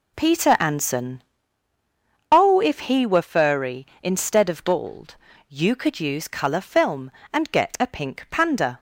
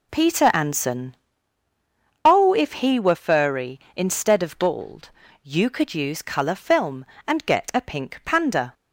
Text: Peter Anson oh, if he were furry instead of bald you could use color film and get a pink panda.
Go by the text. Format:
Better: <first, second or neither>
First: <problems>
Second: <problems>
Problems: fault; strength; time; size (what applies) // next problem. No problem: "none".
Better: neither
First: pauses between "Anson" and "oh"; at 1.2 s; 1.0 s long // pauses between "bald" and "you"; slight; at 5.1 s; 0.34 s long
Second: pauses between "Anson" and "oh"; at 1.1 s; 1.0 s long // pauses between "bald" and "you"; slight; at 5.0 s; 0.34 s long